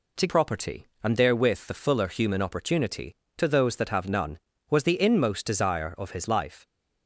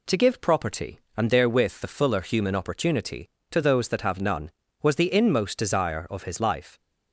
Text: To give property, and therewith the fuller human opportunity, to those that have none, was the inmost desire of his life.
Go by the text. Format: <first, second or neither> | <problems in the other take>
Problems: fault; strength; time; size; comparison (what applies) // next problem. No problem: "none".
second | skips "give"; at 0.2 s